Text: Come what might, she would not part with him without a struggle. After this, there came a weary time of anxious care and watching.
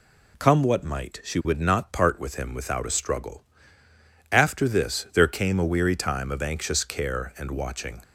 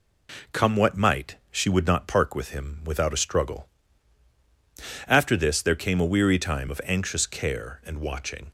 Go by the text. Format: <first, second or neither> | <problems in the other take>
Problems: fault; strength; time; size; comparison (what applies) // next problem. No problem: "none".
first | says "park" for "part"; at 2.0 s